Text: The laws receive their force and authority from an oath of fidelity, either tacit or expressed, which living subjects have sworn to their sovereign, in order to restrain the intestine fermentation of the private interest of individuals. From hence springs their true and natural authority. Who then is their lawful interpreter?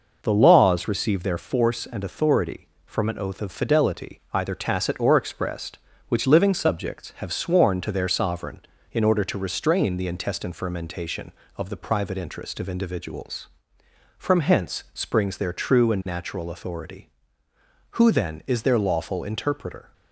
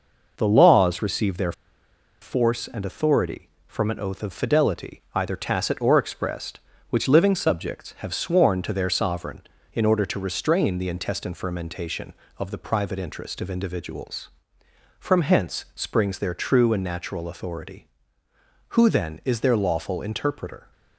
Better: first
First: none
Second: pauses between "their" and "force"; noticeable; at 1.5 s; 0.69 s long

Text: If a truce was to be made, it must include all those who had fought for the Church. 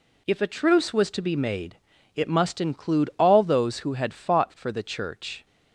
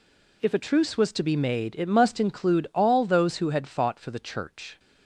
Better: neither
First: none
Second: none

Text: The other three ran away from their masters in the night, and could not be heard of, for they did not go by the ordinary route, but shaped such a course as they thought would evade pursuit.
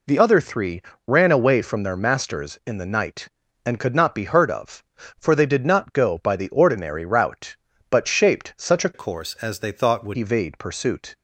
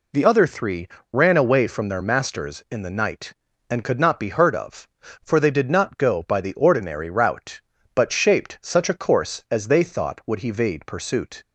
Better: second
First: pauses between "three" and "ran"; slight; at 0.8 s; 0.26 s long // changes voice from "course" to "would"; from 8.9 to 10.1 s; 1.2 s long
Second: pauses between "three" and "ran"; slight; at 0.8 s; 0.26 s long

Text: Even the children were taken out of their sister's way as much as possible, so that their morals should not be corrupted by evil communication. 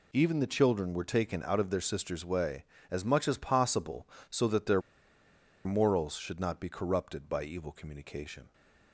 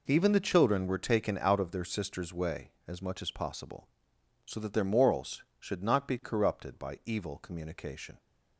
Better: second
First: pauses between "their" and "morals"; noticeable; at 4.8 s; 0.83 s long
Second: none

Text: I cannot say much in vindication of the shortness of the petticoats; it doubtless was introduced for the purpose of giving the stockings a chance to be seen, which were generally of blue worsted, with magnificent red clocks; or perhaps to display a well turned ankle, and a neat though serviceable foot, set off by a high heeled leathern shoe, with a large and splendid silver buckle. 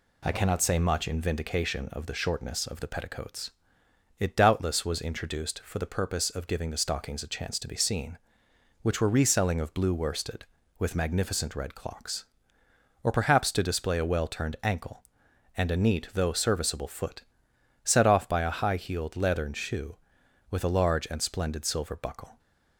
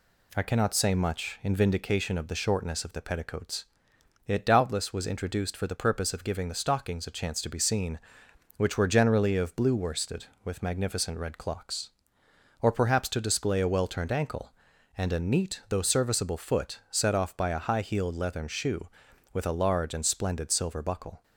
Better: second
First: says "reselling" for "generally"; at 9.0 s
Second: none

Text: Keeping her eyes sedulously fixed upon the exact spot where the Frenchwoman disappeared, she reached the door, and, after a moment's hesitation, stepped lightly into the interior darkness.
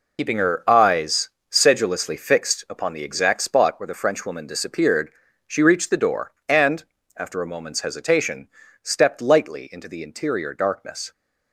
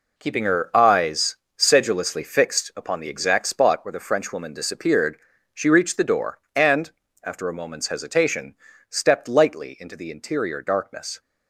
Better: second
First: loses the start of "Keeping"; at 0.1 s; 75 ms // pauses between "eyes" and "sedulously"; slight; at 1.2 s; 0.22 s long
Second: pauses between "eyes" and "sedulously"; slight; at 1.3 s; 0.22 s long

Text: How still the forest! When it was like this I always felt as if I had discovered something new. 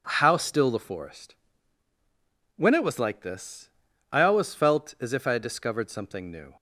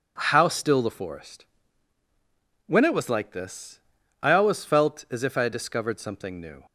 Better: neither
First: pauses between "this" and "I"; at 3.6 s; 0.42 s long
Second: pauses between "this" and "I"; at 3.7 s; 0.42 s long

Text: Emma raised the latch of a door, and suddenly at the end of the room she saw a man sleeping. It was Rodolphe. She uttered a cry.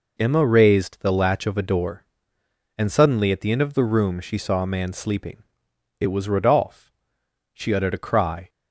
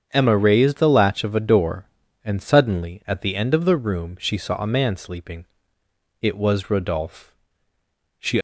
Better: first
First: none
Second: starts louder than the rest; strong; until 1.1 s; 7.5 dB // stops before "uttered a cry"; at 8.3 s

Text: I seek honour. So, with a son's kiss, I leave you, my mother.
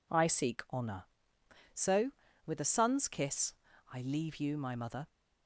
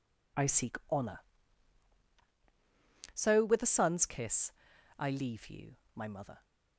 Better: neither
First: none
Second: none

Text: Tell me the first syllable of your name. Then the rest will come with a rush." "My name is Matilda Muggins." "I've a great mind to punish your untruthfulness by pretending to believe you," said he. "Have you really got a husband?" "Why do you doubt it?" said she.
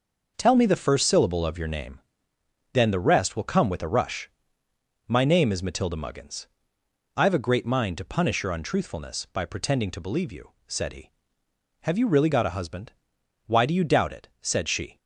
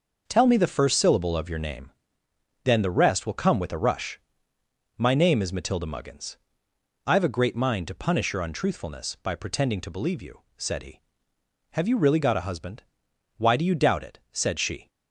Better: neither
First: none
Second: none

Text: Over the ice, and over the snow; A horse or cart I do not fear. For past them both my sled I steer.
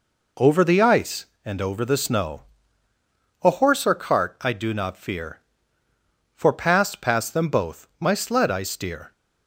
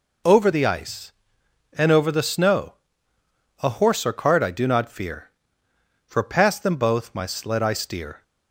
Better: second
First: says "past" twice; at 7.0 s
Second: none

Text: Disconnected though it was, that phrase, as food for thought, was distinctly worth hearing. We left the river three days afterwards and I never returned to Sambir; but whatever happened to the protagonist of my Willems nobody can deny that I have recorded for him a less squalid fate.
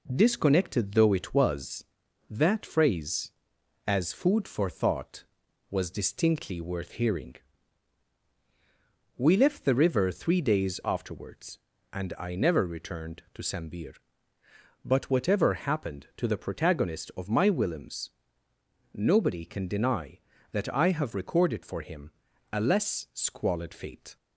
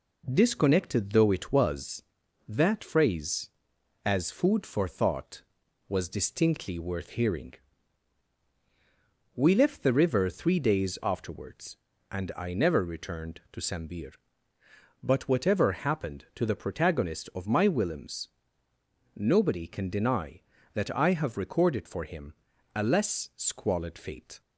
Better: neither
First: pauses between "Willems" and "nobody"; noticeable; at 18.1 s; 0.84 s long // pauses between "him" and "a"; at 22.1 s; 0.42 s long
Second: pauses between "Willems" and "nobody"; noticeable; at 18.2 s; 0.87 s long // pauses between "him" and "a"; at 22.3 s; 0.42 s long

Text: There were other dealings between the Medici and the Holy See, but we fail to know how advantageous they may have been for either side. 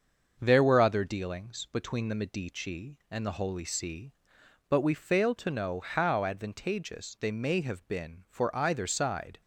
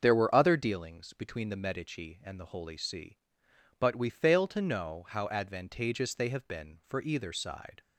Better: first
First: starts louder than the rest; until 1.4 s; 6.5 dB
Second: starts louder than the rest; until 1.0 s; 6.5 dB // skips "may"; at 6.2 s

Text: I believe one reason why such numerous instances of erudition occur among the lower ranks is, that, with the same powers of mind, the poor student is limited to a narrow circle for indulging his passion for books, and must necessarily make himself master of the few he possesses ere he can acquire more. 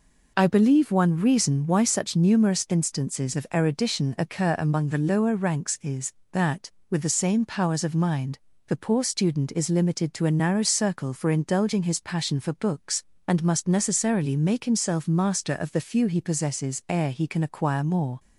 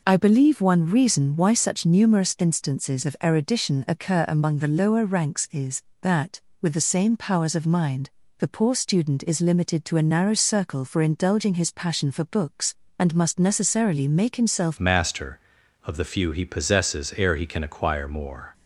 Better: first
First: none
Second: changes voice at "master"; from 14.7 s on; 3.8 s long

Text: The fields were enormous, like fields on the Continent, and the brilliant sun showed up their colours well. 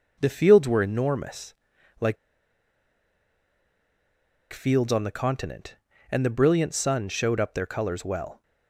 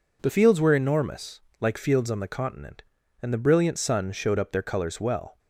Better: second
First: pauses between "like" and "fields"; strong; at 2.1 s; 2.3 s long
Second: none

